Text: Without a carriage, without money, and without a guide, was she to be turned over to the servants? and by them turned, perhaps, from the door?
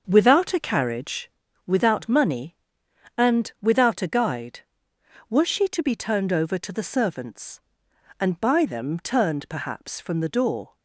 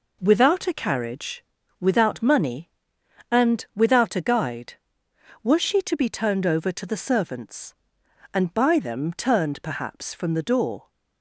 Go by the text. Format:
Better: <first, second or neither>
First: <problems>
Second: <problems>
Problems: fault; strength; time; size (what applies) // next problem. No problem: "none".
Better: second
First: starts louder than the rest; until 1.4 s; 6 dB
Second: none